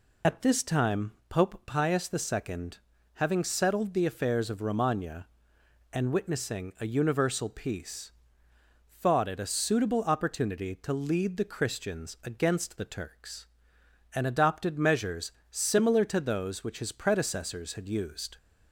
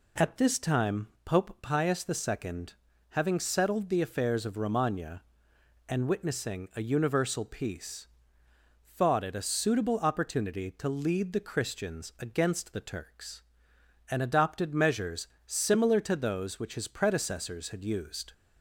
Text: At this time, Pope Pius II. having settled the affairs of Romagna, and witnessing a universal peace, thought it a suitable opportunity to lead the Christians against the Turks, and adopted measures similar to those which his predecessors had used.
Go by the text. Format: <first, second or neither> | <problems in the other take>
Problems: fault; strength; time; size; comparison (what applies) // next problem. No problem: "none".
second | loses the start of "At"; at 0.2 s; 50 ms // pauses between "measures" and "similar"; slight; at 15.3 s; 0.18 s long; slight in the second